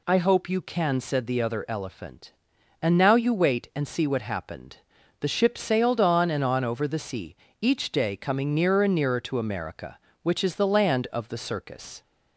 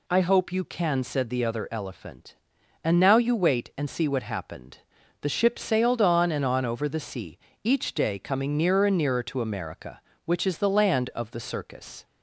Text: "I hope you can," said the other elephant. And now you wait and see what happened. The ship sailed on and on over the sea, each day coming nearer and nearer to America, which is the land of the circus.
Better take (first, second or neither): neither